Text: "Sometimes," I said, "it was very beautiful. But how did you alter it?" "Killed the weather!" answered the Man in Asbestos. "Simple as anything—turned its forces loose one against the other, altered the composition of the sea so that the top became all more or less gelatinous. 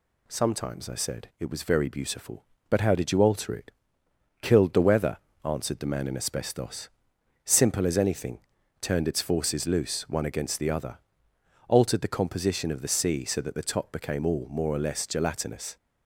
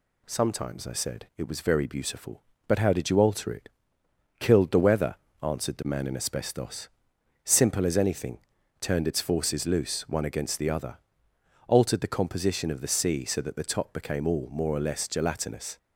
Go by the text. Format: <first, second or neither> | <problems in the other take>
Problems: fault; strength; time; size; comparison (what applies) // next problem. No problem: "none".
neither | none